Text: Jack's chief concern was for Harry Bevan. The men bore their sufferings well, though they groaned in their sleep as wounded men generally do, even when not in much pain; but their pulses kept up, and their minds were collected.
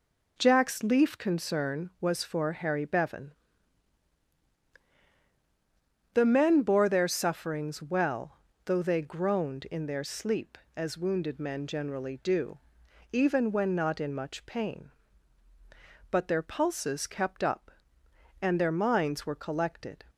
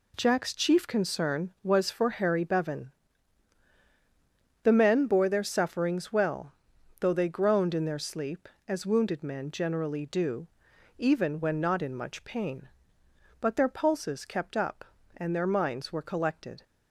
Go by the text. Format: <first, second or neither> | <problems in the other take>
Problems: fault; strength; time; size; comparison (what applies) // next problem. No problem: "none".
second | says "leaf" for "chief"; at 0.8 s